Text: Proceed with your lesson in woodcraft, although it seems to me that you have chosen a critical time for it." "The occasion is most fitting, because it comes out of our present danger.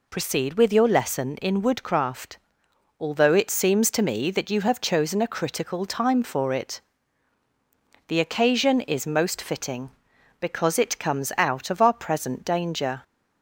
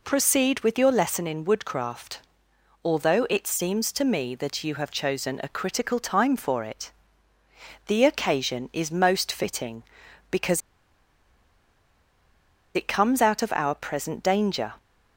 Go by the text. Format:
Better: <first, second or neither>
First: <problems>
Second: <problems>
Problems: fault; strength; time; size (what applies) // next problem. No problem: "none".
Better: first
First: none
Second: pauses between "because" and "it"; strong; at 10.6 s; 2.1 s long